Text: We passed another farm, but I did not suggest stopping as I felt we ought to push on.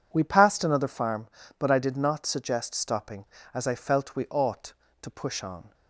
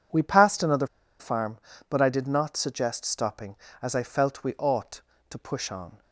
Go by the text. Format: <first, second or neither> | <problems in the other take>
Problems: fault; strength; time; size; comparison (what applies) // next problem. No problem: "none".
first | pauses between "another" and "farm"; slight; at 0.8 s; 0.31 s long